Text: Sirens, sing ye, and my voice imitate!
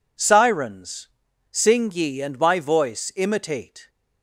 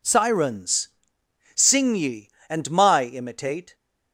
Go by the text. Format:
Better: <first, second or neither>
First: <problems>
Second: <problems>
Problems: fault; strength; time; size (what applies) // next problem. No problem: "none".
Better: first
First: none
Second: skips "voice"; at 3.0 s